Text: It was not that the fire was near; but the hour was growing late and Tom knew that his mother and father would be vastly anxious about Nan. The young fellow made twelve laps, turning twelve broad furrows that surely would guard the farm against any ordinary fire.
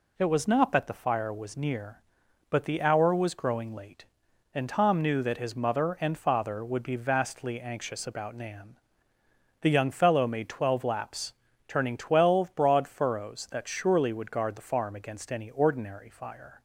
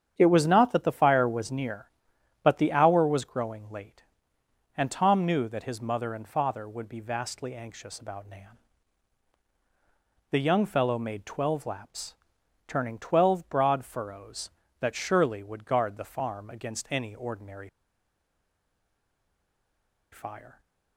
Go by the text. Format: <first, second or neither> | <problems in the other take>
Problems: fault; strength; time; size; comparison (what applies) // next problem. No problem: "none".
first | starts louder than the rest; strong; until 1.1 s; 8.5 dB // pauses between "ordinary" and "fire"; strong; at 17.6 s; 2.4 s long